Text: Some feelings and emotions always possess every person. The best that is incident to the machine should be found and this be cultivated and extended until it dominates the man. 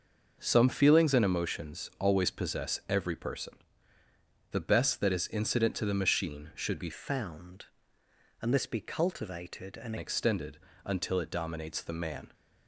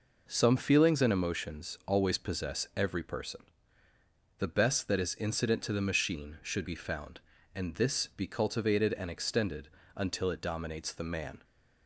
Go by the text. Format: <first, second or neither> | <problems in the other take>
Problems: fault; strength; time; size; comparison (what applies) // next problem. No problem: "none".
second | changes voice from "found" to "and"; from 6.9 to 9.9 s; 3.0 s long // pauses between "extended" and "until"; slight; at 10.5 s; 0.28 s long; slight in the second